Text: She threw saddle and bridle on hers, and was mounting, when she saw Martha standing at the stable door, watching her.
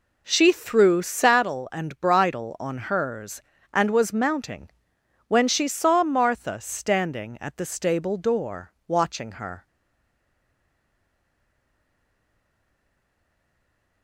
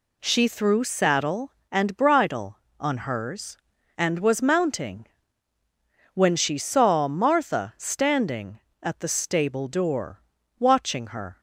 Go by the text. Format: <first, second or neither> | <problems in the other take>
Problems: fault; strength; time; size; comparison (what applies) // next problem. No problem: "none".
second | stays silent after the last word; strong; from 9.6 s on; 4.4 s long